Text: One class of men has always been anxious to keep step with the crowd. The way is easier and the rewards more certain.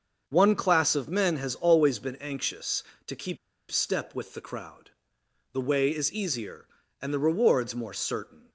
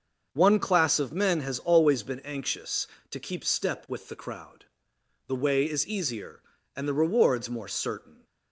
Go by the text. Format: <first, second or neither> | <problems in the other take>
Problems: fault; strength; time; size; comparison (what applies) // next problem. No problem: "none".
second | starts louder than the rest; until 1.2 s; 7 dB; also in the second // pauses between "keep" and "step"; slight; at 3.3 s; 0.34 s long